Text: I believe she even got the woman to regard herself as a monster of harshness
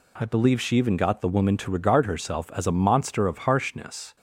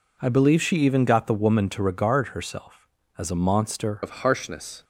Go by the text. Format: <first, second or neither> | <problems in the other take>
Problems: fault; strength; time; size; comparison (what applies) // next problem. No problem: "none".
first | changes voice at "of"; from 4.0 s on; 0.8 s long